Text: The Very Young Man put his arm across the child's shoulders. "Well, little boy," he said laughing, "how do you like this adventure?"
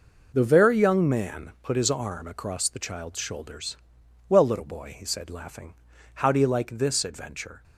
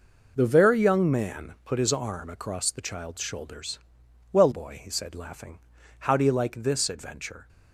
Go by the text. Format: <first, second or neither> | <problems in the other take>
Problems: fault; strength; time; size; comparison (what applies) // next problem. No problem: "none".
first | skips "little"; at 4.5 s